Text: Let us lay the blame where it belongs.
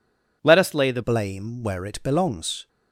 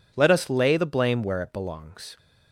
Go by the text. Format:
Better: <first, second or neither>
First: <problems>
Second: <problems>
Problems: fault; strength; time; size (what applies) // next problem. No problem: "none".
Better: second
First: changes voice at "blame"; from 1.0 s on; 1.6 s long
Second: none